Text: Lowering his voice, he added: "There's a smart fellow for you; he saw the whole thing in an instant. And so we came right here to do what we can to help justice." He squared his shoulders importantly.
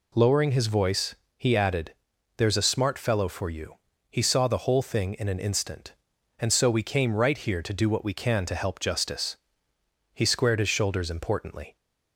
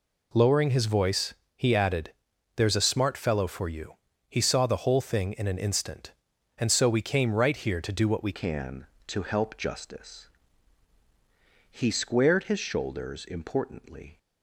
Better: first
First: none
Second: changes voice at "can"; from 8.3 s on; 5.8 s long

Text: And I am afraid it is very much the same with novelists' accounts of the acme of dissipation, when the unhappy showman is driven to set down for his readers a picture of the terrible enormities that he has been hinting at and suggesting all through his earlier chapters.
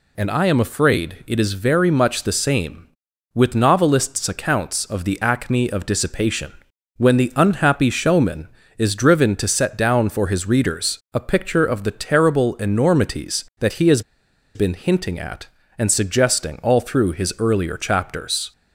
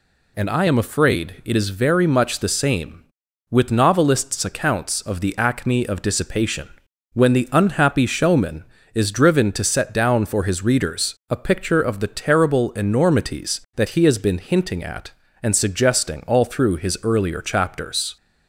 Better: second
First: pauses between "has" and "been"; noticeable; at 14.0 s; 0.54 s long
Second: none

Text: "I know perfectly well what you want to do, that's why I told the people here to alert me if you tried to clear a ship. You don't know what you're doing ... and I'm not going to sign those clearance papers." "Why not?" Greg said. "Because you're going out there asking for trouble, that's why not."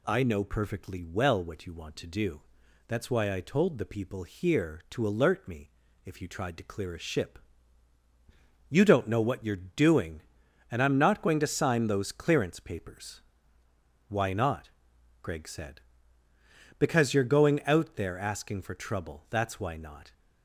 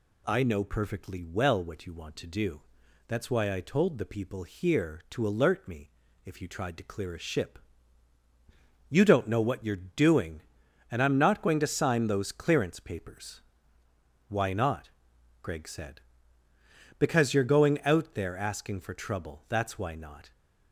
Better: neither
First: pauses between "me" and "if"; slight; at 5.6 s; 0.34 s long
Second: pauses between "me" and "if"; slight; at 5.8 s; 0.34 s long

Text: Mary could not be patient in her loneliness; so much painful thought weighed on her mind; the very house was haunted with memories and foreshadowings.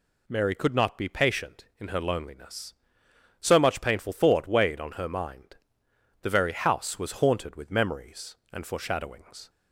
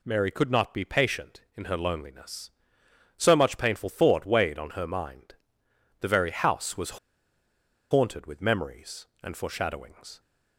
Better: first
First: none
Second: pauses between "was" and "haunted"; noticeable; at 6.9 s; 0.93 s long

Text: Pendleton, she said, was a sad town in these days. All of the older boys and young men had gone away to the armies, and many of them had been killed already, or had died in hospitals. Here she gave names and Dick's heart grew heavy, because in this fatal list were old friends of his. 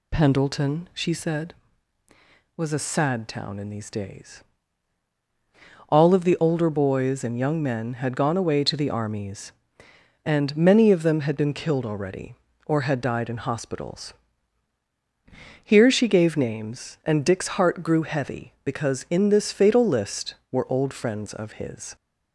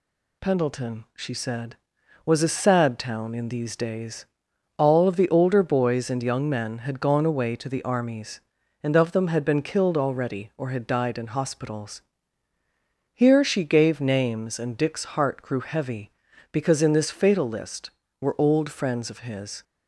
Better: first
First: none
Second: skips "many"; at 8.9 s

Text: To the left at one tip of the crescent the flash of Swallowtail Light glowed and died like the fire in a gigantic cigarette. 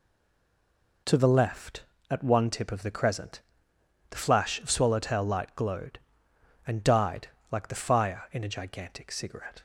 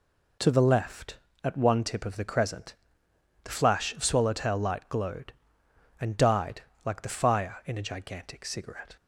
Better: second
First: stays silent before the first word; until 1.0 s; 1.0 s long // pauses between "crescent" and "the"; noticeable; at 3.4 s; 0.68 s long // pauses between "died" and "like"; slight; at 7.2 s; 0.22 s long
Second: pauses between "crescent" and "the"; noticeable; at 2.7 s; 0.68 s long // pauses between "died" and "like"; slight; at 6.6 s; 0.22 s long

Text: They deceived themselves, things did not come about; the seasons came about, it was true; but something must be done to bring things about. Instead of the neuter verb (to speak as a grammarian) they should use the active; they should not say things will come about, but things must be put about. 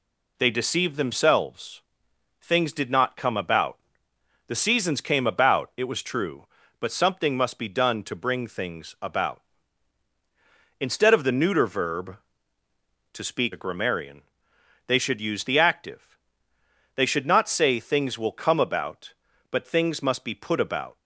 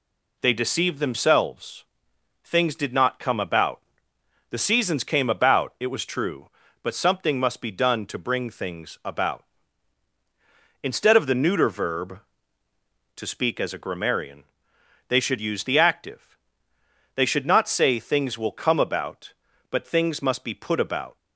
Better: second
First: skips "as"; at 13.5 s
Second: none

